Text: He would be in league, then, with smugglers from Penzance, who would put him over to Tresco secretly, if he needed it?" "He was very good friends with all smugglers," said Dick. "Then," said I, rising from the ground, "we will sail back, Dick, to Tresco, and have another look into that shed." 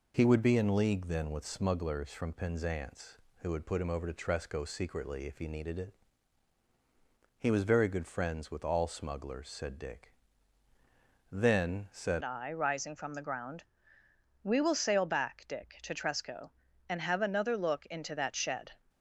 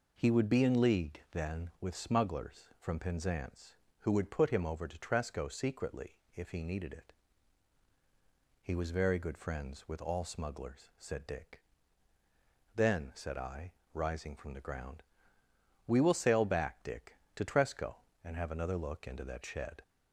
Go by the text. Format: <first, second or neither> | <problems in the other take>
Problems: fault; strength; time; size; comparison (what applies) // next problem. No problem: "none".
second | changes voice at "I"; from 12.2 s on; 6.5 s long